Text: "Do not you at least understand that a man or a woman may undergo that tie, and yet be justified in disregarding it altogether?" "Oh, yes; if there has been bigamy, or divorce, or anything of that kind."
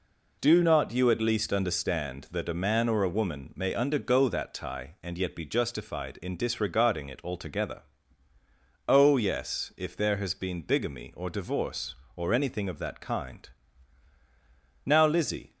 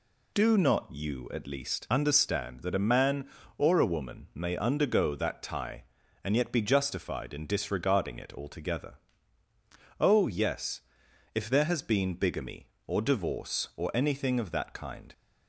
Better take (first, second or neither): second